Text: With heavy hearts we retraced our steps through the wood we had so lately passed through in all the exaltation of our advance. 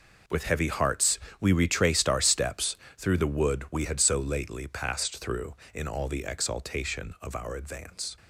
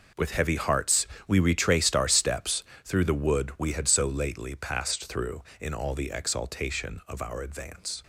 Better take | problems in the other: neither | pauses between "hearts" and "we"; slight; the same in both // pauses between "steps" and "through"; slight; the same in both

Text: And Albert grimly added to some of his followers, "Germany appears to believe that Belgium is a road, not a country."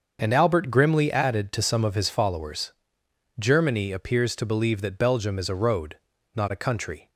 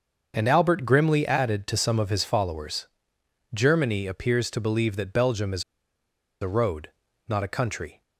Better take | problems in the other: first | starts louder than the rest; until 1.3 s; 6.5 dB; also in the first // pauses between "is" and "a"; noticeable; at 5.6 s; 0.78 s long

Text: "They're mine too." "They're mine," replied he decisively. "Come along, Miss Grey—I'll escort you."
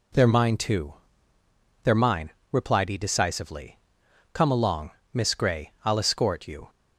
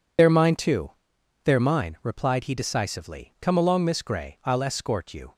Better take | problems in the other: first | loses the start of "They're"; at 0.1 s; 50 ms

